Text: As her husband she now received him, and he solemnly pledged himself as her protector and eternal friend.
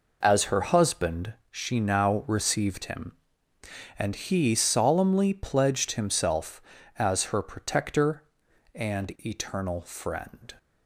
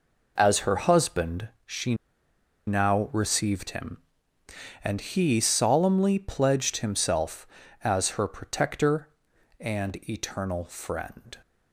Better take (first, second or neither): first